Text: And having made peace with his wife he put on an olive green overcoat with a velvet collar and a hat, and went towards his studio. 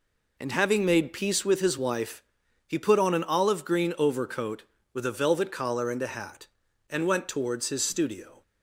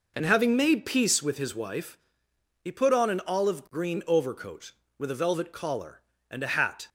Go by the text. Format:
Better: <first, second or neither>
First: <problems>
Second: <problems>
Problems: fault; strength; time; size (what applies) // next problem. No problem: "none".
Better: first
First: pauses between "wife" and "he"; noticeable; at 2.2 s; 0.46 s long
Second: pauses between "wife" and "he"; noticeable; at 1.9 s; 0.66 s long // stops before "and went towards his studio"; at 6.8 s